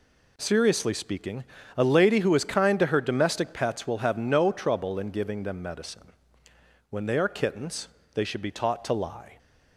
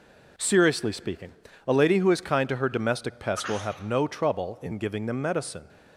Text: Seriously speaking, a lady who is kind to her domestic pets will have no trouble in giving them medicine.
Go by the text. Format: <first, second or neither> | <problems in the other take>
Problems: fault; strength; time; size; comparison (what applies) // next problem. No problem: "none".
second | goes on to say "When they are Kittens they should be taught to lie"; strong; from 6.8 s on; 2.4 s long